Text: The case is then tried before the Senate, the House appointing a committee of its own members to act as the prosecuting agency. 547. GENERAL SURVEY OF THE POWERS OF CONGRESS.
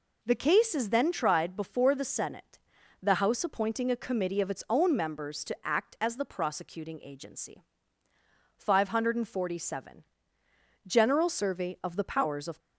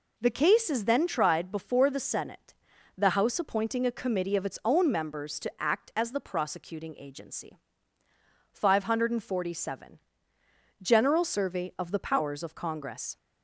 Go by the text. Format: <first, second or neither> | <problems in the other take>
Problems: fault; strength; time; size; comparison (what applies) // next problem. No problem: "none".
second | stops before "CONGRESS"; at 12.5 s